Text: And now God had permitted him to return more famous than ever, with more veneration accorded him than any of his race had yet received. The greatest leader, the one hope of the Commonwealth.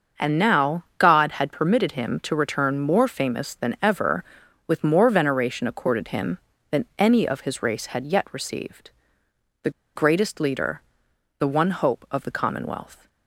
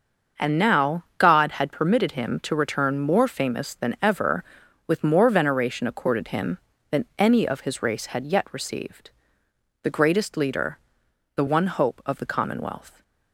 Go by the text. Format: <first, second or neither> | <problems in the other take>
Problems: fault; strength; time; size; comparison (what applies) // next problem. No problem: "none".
second | starts louder than the rest; until 1.3 s; 6.5 dB; also in the second // pauses between "The" and "greatest"; slight; at 9.7 s; 0.25 s long